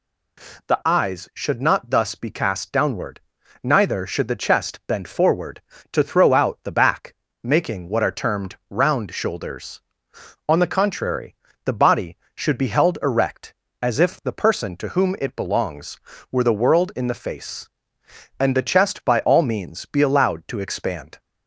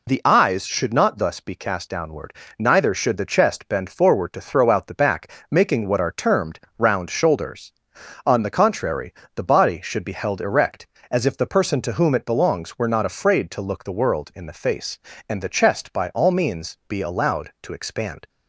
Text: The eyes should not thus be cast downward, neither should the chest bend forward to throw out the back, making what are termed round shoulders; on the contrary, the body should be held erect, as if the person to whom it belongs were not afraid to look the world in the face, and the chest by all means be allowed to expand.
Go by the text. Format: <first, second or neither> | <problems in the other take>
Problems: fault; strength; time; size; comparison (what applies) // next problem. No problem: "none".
second | pauses between "termed" and "round"; slight; at 8.5 s; 0.16 s long; slight in the second // skips "not afraid to look"; at 16.4 s